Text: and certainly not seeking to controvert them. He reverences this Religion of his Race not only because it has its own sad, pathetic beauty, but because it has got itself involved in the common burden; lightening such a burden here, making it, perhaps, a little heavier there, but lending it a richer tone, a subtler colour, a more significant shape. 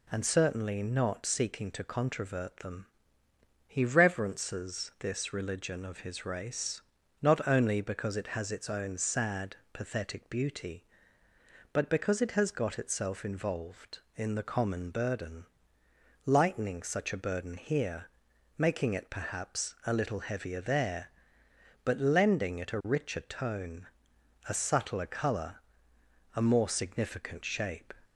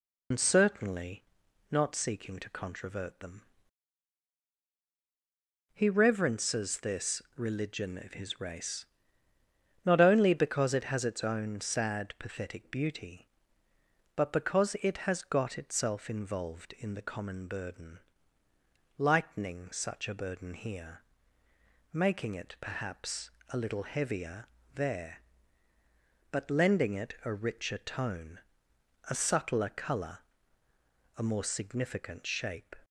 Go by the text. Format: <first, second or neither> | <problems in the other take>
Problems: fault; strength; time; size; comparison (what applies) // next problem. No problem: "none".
first | loses the start of "and"; at 0.3 s; 65 ms // pauses between "certainly" and "not"; noticeable; at 1.2 s; 0.46 s long // pauses between "Race" and "not"; at 8.8 s; 1.0 s long; also in the first // pauses between "heavier" and "there"; slight; at 24.4 s; 0.28 s long